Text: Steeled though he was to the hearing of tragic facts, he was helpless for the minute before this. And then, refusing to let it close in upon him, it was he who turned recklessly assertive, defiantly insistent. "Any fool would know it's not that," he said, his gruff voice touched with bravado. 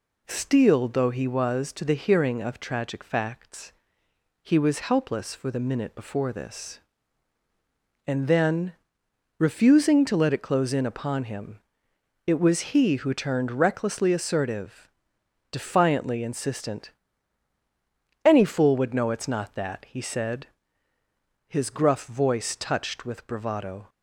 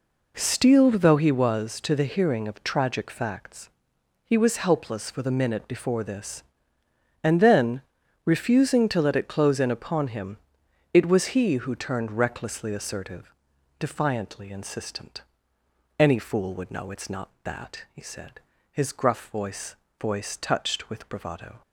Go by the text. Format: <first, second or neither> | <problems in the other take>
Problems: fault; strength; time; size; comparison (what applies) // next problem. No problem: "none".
first | says "voice" twice; at 19.9 s